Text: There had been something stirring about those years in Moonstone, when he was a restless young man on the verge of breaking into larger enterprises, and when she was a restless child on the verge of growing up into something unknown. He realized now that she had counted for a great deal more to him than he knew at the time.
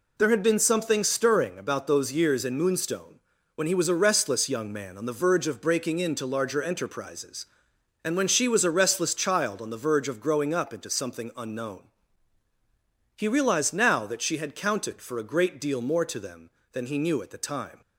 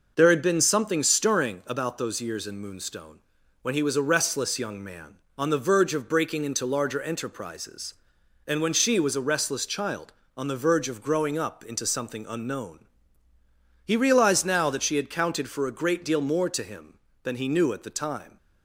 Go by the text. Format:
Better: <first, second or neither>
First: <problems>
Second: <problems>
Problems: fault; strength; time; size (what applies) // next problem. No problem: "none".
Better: second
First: says "them" for "him"; at 16.1 s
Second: none